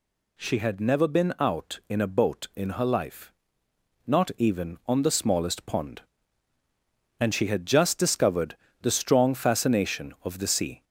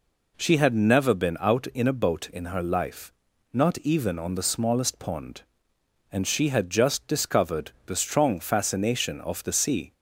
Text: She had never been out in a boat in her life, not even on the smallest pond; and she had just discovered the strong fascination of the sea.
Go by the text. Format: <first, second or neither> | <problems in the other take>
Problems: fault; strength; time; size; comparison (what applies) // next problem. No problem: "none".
second | gets louder; slight; throughout; 2 dB // pauses between "discovered" and "the"; slight; at 8.5 s; 0.26 s long; slight in the second